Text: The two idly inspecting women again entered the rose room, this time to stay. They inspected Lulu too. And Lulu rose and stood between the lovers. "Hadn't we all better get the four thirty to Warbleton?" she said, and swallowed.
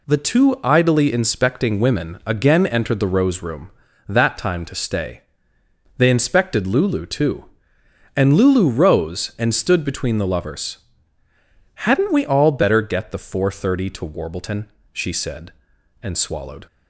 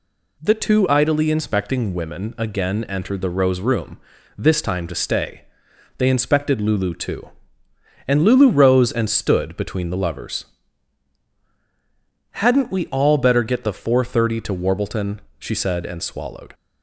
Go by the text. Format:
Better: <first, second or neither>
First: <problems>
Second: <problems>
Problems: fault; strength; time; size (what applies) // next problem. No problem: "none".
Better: second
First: says "that" for "this"; at 4.0 s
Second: none